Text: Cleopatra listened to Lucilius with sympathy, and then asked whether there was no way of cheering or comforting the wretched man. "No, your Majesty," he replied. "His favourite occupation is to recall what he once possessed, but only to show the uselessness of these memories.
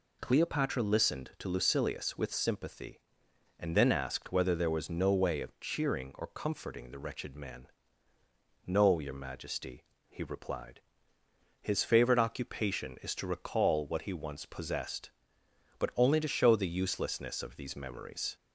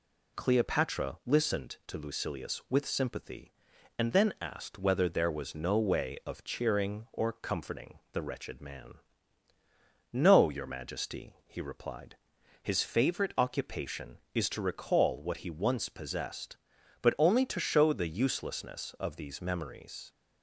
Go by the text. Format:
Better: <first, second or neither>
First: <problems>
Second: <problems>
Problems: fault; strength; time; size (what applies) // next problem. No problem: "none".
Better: neither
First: none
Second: none